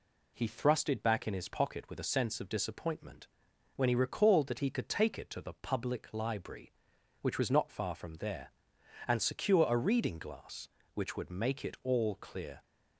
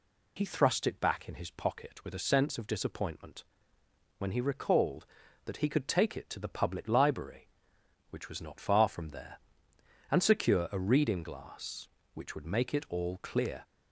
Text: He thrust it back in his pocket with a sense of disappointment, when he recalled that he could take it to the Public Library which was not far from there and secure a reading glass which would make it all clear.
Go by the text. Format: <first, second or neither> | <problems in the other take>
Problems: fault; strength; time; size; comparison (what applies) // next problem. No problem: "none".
neither | none